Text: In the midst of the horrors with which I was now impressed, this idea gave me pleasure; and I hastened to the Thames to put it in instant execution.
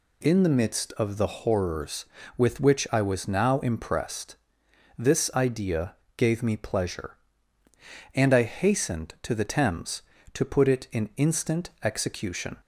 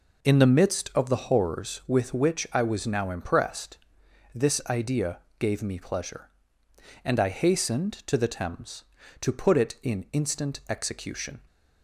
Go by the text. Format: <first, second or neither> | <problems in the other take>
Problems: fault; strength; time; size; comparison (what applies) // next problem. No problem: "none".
neither | pauses between "idea" and "gave"; slight; the same in both